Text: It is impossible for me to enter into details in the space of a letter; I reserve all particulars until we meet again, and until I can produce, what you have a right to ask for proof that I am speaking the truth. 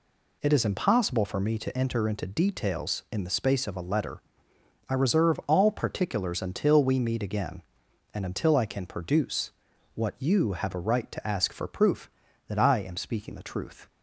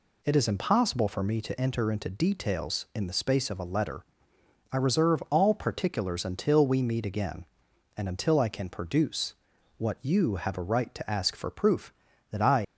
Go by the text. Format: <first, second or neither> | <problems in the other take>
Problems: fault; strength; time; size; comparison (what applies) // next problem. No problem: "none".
first | stops before "am speaking the truth"; at 12.6 s